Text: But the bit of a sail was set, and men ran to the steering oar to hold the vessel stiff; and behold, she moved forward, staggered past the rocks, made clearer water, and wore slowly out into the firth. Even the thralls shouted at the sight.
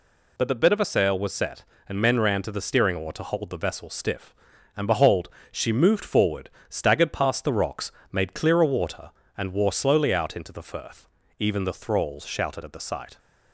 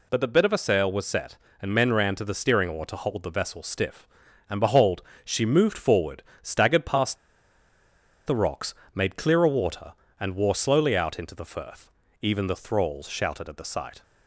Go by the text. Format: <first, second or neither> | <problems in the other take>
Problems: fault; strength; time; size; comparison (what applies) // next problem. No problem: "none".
first | pauses between "past" and "the"; at 7.1 s; 1.1 s long